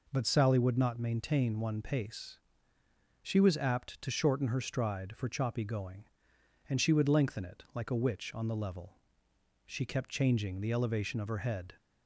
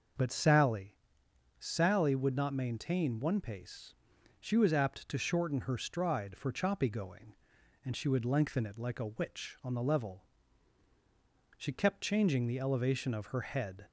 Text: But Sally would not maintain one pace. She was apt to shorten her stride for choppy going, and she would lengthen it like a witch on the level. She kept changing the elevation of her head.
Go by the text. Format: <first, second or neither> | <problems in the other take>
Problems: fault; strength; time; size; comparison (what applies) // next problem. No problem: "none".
first | says "Sally" twice; at 1.5 s